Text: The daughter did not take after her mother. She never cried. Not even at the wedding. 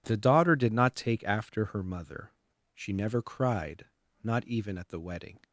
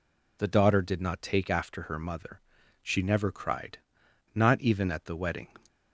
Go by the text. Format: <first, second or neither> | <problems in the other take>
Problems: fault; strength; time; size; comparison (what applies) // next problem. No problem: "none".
neither | none